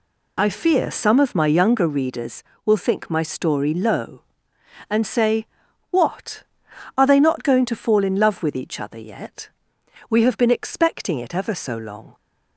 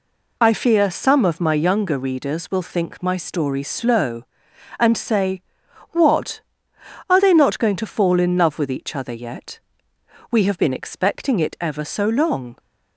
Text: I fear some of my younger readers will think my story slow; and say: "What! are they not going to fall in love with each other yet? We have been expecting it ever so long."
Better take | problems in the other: second | says "low" for "slow"; at 3.7 s

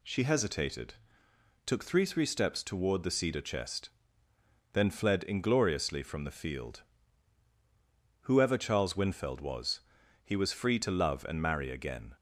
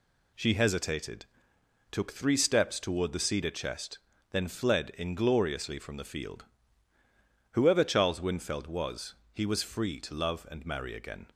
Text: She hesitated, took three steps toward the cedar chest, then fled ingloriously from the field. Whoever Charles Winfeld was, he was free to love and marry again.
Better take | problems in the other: second | says "three" twice; at 2.0 s

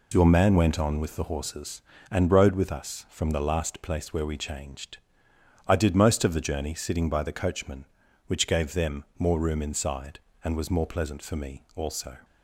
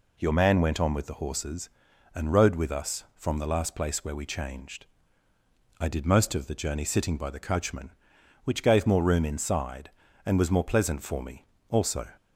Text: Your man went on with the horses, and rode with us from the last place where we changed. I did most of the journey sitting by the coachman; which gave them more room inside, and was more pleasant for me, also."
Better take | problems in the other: first | skips "them"; at 8.8 s

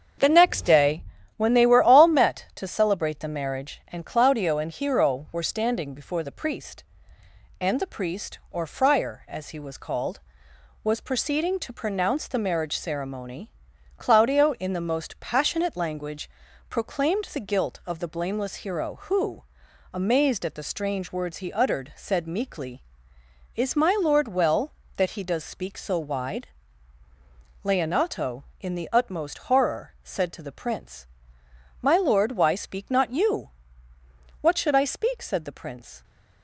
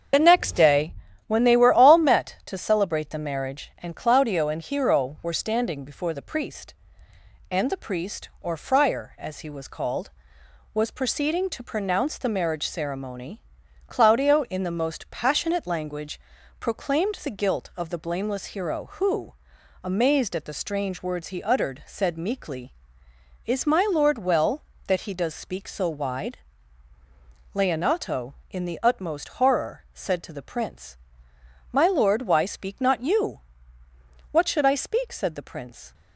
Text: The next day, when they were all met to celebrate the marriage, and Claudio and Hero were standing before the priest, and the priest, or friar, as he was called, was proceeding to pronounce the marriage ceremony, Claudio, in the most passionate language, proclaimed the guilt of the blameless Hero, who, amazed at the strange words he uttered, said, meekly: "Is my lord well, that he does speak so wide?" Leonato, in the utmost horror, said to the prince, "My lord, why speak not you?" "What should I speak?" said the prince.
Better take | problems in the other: first | loses the start of "The"; at 0.1 s; 40 ms // starts louder than the rest; until 1.4 s; 7 dB; also in the first

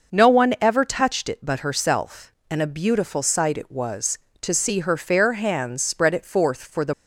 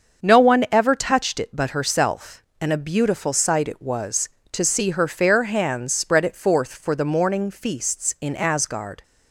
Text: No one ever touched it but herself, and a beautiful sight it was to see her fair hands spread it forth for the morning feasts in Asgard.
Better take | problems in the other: second | starts louder than the rest; noticeable; until 1.2 s; 6 dB; also in the second // stops before "morning feasts in Asgard"; at 6.9 s

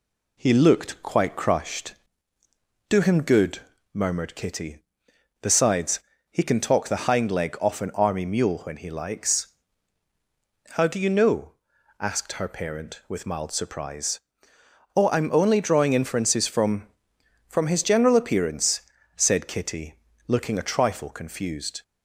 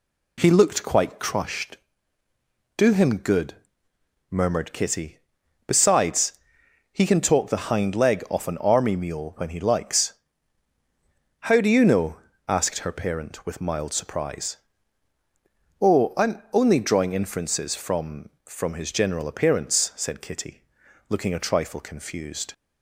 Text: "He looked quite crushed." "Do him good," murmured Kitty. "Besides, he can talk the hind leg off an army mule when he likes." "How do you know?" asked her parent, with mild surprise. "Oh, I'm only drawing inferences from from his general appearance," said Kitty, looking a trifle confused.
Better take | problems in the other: neither | none

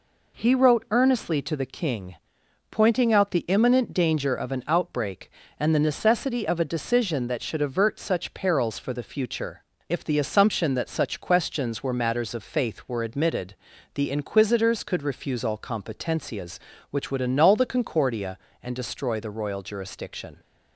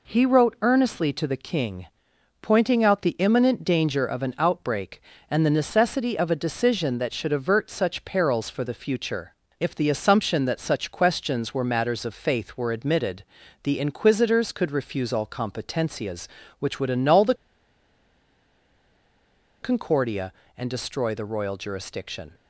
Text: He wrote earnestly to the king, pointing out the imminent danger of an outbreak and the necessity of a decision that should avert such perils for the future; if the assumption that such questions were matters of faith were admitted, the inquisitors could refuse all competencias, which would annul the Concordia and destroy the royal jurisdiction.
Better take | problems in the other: first | pauses between "the" and "Concordia"; strong; at 17.3 s; 2.2 s long

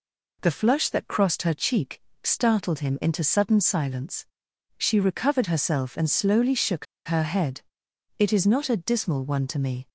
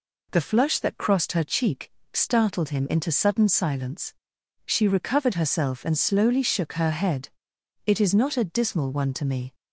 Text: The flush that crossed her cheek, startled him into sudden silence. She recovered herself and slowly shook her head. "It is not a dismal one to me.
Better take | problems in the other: second | pauses between "shook" and "her"; slight; at 6.8 s; 0.20 s long

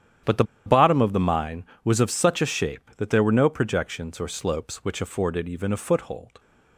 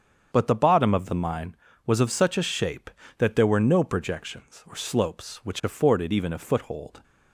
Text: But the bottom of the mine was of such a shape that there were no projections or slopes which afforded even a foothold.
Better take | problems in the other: second | starts louder than the rest; strong; until 1.4 s; 10 dB; strong in the second // pauses between "the" and "bottom"; slight; at 0.4 s; 0.22 s long

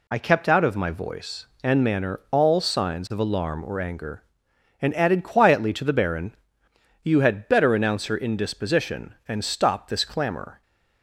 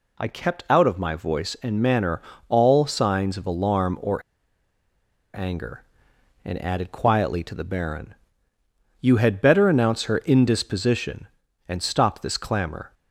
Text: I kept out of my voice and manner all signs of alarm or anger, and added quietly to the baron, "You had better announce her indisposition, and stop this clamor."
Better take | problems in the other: first | pauses between "manner" and "all"; slight; at 2.2 s; 0.26 s long // pauses between "or" and "anger"; at 4.2 s; 1.1 s long

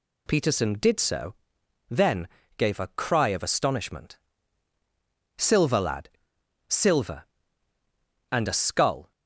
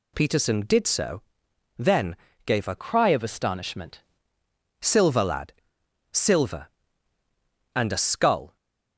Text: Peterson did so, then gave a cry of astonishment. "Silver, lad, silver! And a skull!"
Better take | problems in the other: first | pauses between "then" and "gave"; slight; at 2.1 s; 0.32 s long; slight in the first // changes voice from "cry" to "astonishment"; from 2.7 to 4.0 s; 1.3 s long

